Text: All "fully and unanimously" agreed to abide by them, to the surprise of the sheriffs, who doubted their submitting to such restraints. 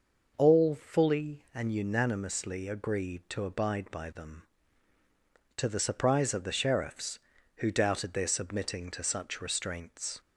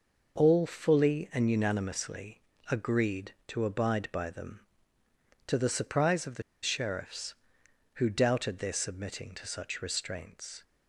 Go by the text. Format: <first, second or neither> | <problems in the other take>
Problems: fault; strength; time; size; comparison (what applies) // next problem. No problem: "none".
first | pauses between "unanimously" and "agreed"; slight; at 2.4 s; 0.26 s long // pauses between "the" and "sheriffs"; slight; at 6.4 s; 0.20 s long